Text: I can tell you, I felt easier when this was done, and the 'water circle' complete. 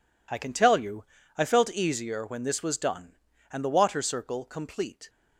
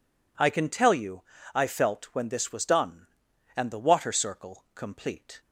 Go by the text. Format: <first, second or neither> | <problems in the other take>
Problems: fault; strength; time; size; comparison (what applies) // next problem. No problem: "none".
first | skips "easier"; at 2.1 s